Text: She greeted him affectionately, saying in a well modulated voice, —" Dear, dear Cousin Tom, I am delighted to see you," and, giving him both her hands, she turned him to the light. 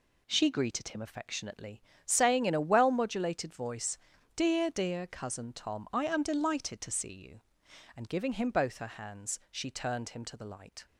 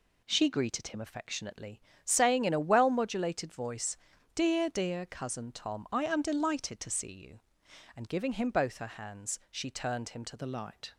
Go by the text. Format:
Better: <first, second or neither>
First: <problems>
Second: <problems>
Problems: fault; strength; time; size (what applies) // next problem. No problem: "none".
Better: first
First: none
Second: changes voice at "the"; from 10.3 s on; 0.6 s long